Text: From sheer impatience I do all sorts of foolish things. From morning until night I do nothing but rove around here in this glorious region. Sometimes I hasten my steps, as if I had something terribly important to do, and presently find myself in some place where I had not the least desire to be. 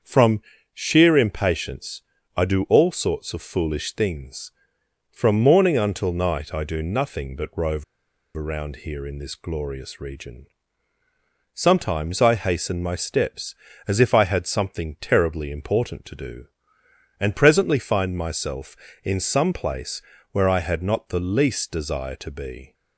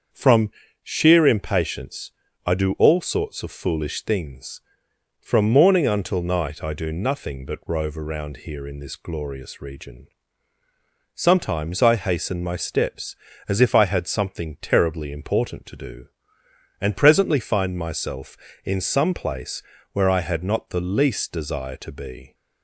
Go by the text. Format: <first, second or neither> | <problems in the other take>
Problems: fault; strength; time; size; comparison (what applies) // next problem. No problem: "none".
second | starts louder than the rest; until 1.3 s; 7 dB; also in the second // pauses between "From" and "sheer"; slight; at 0.4 s; 0.32 s long; slight in the second // pauses between "impatience" and "I"; slight; at 2.0 s; 0.34 s long; slight in the second // pauses between "rove" and "around"; noticeable; at 7.8 s; 0.52 s long // pauses between "place" and "where"; slight; at 20.0 s; 0.30 s long; slight in the second